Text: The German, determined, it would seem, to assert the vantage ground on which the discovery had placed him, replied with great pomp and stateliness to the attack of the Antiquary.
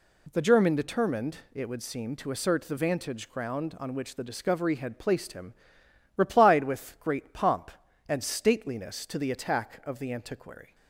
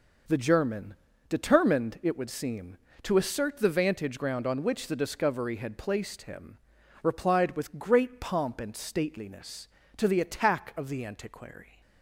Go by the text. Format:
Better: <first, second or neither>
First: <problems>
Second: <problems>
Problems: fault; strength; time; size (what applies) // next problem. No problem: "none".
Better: neither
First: none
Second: none